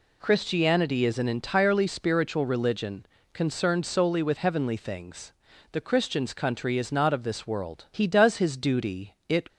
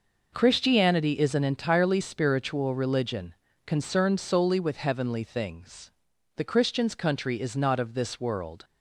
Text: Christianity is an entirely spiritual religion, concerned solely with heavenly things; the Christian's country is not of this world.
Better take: second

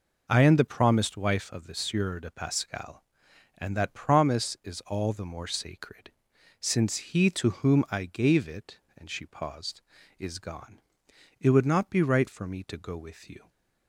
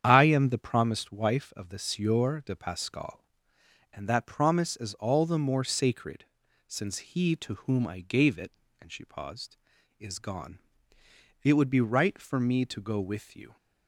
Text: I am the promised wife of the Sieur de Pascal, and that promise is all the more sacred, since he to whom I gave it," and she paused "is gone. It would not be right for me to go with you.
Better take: first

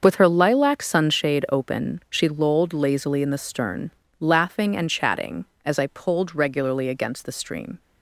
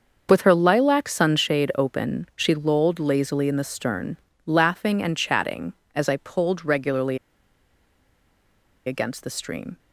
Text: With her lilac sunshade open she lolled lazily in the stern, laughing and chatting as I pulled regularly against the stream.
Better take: first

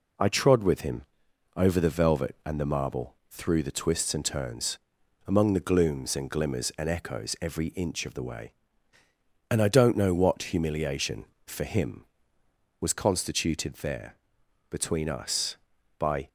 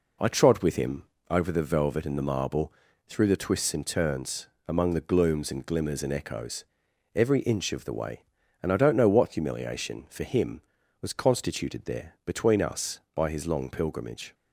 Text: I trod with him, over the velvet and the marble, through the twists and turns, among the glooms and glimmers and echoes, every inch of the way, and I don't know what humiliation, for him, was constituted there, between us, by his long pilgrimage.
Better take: second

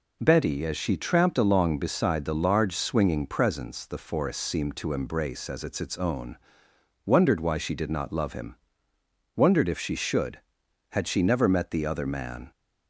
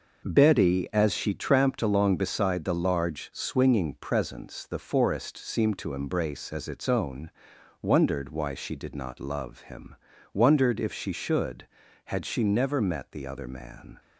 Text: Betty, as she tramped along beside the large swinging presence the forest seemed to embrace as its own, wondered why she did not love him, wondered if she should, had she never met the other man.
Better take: second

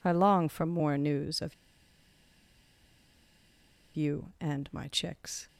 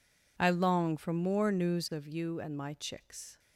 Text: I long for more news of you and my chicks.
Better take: second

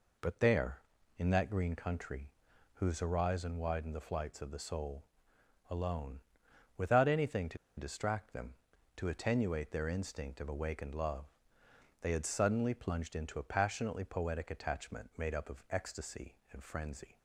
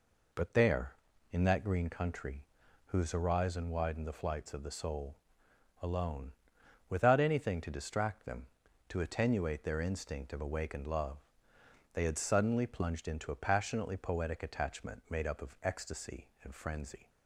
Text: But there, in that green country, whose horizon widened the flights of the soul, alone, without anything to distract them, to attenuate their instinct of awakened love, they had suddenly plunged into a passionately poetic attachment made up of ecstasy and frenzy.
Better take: second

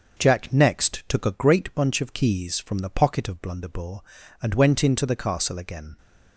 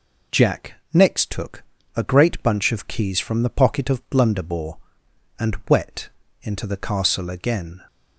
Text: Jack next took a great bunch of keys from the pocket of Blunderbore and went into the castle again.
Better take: first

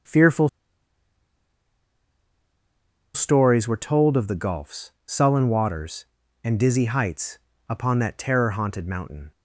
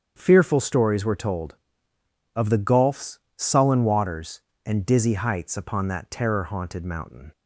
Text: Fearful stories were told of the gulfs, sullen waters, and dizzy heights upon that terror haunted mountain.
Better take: second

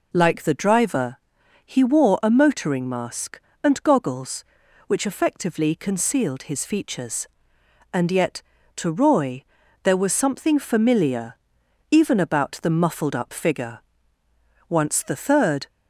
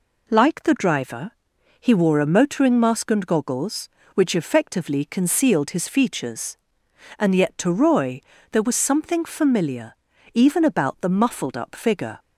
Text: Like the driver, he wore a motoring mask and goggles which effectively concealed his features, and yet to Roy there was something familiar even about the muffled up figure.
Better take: second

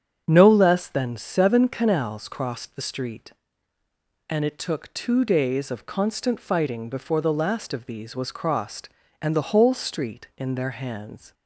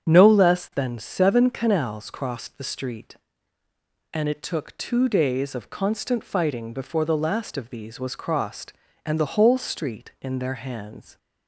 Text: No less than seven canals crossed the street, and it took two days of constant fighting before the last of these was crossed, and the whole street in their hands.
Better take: neither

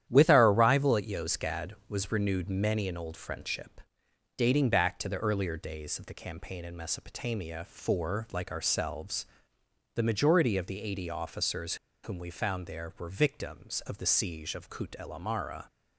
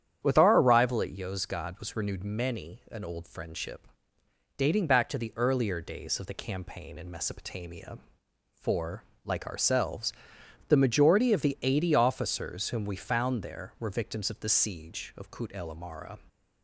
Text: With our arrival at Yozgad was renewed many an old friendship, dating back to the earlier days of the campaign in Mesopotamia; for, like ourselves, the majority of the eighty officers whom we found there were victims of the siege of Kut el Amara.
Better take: second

